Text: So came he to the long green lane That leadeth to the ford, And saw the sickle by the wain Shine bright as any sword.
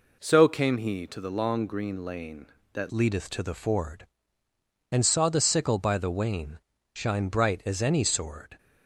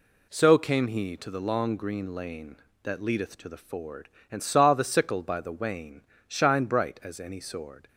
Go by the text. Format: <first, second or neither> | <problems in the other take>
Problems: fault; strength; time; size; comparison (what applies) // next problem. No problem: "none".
second | changes voice at "leadeth"; from 2.9 s on; 5.6 s long // pauses between "wain" and "Shine"; slight; at 6.5 s; 0.32 s long; slight in the second